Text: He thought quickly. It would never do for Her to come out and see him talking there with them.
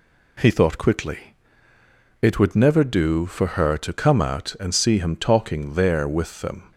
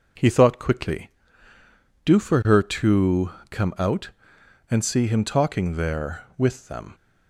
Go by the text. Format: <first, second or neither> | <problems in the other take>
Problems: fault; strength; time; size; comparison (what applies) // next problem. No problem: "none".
first | skips "It would never"; at 1.5 s // pauses between "to" and "come"; slight; at 3.3 s; 0.20 s long